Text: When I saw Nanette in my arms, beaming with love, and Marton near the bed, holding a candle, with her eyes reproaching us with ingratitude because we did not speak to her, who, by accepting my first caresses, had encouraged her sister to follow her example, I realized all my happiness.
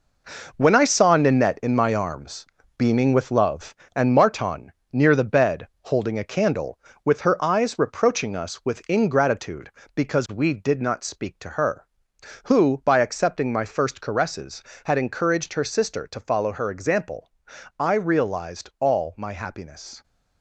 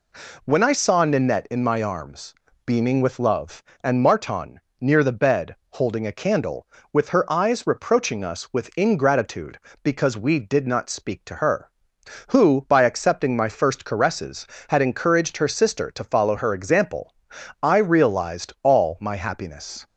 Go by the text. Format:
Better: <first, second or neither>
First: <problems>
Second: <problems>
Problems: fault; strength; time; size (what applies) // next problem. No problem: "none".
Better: second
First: gets quieter; strong; throughout; 8 dB // pauses between "Marton" and "near"; slight; at 4.7 s; 0.18 s long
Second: pauses between "Marton" and "near"; slight; at 4.6 s; 0.18 s long